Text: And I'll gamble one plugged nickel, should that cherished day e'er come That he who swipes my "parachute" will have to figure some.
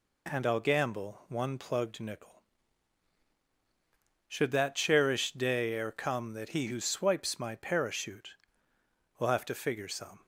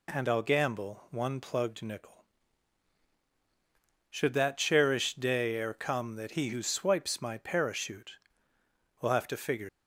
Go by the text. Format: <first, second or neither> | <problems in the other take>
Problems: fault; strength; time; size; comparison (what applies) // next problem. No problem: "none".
first | stops before "some"; at 9.6 s